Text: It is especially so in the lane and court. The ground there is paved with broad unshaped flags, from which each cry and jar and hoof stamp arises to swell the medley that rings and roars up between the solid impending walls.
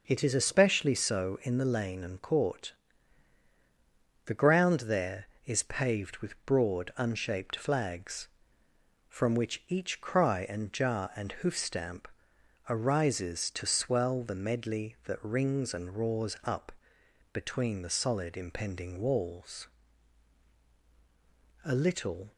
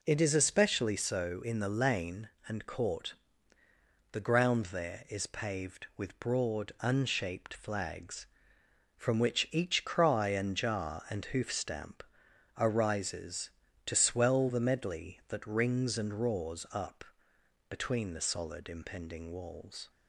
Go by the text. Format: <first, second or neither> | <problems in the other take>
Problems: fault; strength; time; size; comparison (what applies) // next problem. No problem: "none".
second | pauses between "stamp" and "arises"; noticeable; at 12.0 s; 0.62 s long; noticeable in the second // pauses between "up" and "between"; noticeable; at 16.7 s; 0.62 s long; noticeable in the second // goes on to say "A little"; noticeable; from 21.6 s on; 0.68 s long